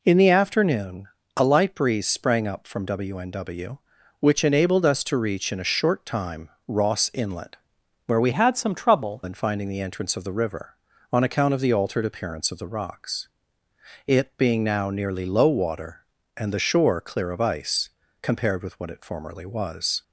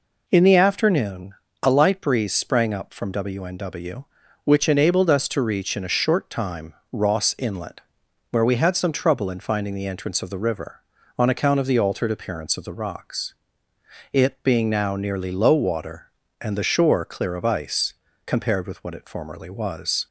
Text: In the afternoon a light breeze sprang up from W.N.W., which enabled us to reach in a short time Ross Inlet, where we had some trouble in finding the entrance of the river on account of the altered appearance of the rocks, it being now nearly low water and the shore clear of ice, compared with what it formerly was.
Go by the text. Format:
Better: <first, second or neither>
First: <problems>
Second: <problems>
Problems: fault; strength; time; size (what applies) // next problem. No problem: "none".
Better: second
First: pauses between "afternoon" and "a"; slight; at 1.0 s; 0.28 s long // pauses between "time" and "Ross"; slight; at 6.4 s; 0.18 s long // changes voice from "had" to "trouble"; from 8.3 to 9.2 s; 0.9 s long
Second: pauses between "afternoon" and "a"; slight; at 1.3 s; 0.28 s long // pauses between "time" and "Ross"; slight; at 6.7 s; 0.18 s long